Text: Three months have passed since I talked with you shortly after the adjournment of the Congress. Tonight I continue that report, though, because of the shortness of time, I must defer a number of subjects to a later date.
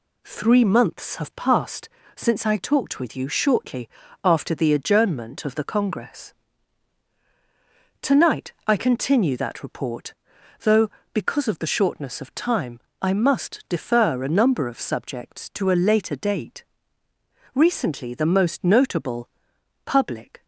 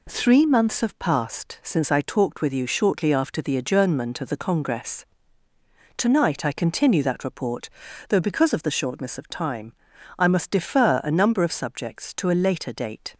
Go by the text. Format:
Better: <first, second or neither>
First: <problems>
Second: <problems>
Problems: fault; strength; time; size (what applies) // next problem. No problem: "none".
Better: second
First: pauses between "passed" and "since"; slight; at 1.8 s; 0.26 s long // pauses between "shortly" and "after"; slight; at 3.8 s; 0.34 s long // goes on to say "Recently the most notable public"; strong; from 17.5 s on; 2.9 s long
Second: none